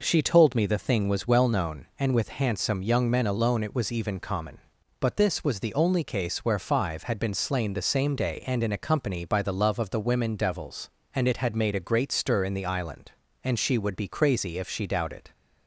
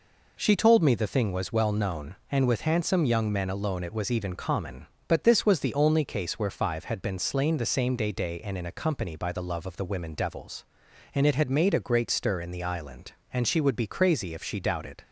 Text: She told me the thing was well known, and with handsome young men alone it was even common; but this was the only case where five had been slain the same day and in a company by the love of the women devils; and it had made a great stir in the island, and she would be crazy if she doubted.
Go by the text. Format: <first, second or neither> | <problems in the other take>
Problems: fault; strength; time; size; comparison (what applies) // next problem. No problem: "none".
first | says "day" twice; at 8.1 s